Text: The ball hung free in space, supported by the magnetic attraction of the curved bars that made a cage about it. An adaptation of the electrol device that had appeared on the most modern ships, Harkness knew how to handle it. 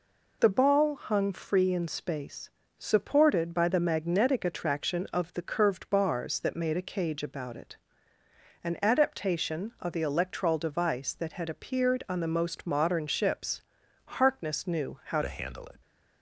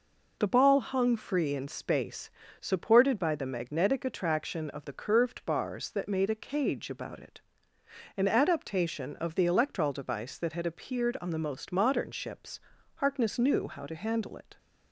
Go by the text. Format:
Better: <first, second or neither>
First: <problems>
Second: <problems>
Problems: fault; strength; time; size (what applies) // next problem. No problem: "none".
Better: second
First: changes voice at "to"; from 15.2 s on; 0.6 s long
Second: none